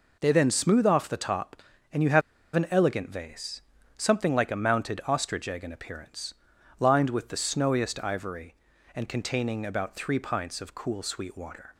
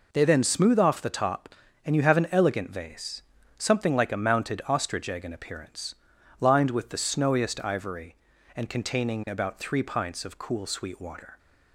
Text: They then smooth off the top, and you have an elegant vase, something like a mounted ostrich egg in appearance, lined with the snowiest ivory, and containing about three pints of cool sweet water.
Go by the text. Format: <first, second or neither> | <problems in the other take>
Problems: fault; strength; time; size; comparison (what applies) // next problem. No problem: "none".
second | pauses between "have" and "an"; slight; at 2.2 s; 0.34 s long